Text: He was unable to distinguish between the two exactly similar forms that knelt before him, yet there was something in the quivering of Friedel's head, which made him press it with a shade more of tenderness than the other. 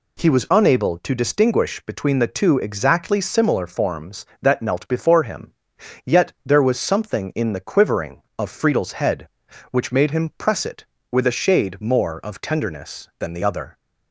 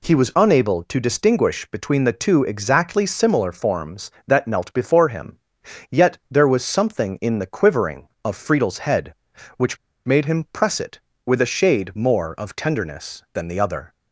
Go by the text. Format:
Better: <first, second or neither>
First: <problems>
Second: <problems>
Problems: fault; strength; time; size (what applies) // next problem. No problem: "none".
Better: first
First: none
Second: pauses between "which" and "made"; slight; at 9.7 s; 0.28 s long